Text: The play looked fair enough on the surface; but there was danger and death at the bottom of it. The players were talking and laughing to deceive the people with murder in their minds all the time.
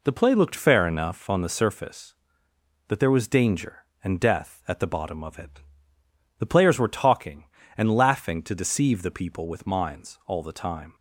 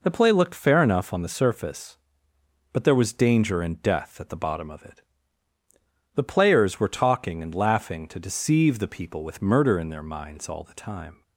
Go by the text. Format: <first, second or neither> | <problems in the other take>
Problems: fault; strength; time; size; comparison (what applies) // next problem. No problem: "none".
second | skips "murder in their"; at 9.6 s